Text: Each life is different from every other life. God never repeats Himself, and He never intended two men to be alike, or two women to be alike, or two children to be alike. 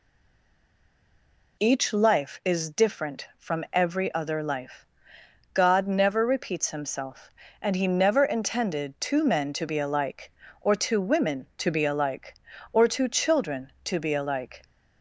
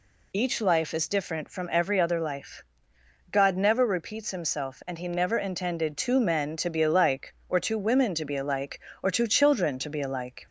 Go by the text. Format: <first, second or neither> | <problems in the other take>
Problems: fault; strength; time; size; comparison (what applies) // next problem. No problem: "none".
second | stays silent before the first word; noticeable; until 1.5 s; 1.5 s long